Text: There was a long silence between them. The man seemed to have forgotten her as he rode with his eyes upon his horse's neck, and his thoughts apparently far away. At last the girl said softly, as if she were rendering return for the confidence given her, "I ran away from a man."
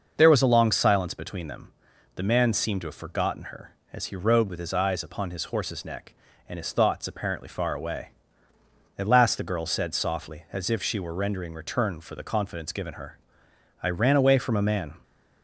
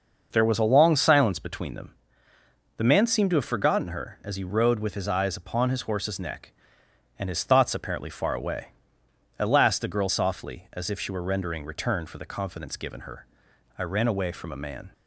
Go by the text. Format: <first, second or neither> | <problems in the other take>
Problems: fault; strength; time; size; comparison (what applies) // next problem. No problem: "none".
first | starts louder than the rest; noticeable; until 1.3 s; 6 dB; noticeable in the first // skips "said"; at 10.0 s